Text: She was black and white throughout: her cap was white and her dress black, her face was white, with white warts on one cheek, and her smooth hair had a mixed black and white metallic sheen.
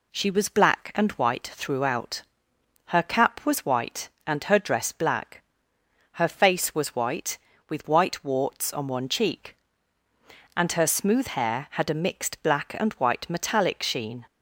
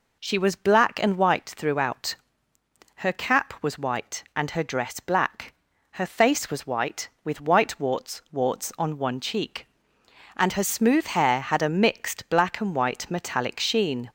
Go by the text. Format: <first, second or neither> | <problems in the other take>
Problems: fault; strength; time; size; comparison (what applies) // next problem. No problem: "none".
first | says "warts" twice; at 8.3 s